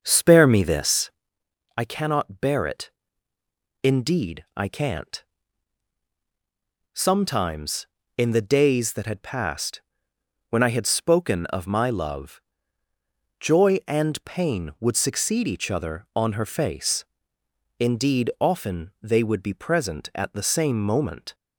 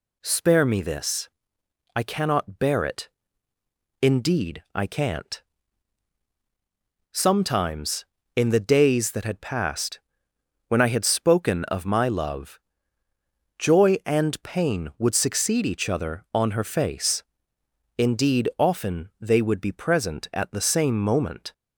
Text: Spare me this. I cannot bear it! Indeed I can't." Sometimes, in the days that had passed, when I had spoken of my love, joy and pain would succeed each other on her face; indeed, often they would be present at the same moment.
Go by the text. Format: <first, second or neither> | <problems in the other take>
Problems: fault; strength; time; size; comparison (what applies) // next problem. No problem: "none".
second | starts louder than the rest; until 1.3 s; 7 dB